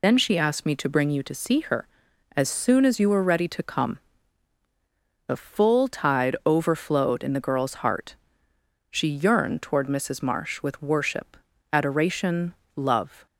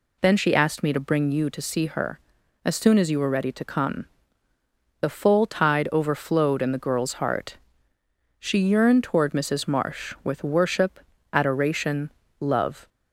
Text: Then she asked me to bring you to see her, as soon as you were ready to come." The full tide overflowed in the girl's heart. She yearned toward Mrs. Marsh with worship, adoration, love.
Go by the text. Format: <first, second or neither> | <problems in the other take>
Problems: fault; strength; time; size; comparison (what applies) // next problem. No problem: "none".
second | loses the start of "Then"; at 0.0 s; 60 ms